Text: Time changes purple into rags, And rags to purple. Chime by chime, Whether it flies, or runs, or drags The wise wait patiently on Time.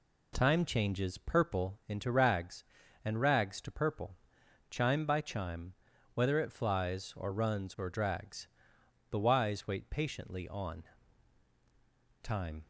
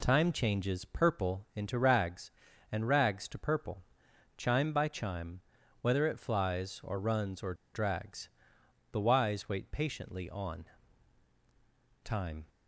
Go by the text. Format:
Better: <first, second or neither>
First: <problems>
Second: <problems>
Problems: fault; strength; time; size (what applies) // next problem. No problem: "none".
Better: first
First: pauses between "drags" and "The"; noticeable; at 8.4 s; 0.62 s long // pauses between "on" and "Time"; strong; at 10.8 s; 1.4 s long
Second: pauses between "or" and "drags"; slight; at 7.5 s; 0.20 s long // pauses between "drags" and "The"; noticeable; at 8.2 s; 0.62 s long // pauses between "on" and "Time"; strong; at 10.6 s; 1.4 s long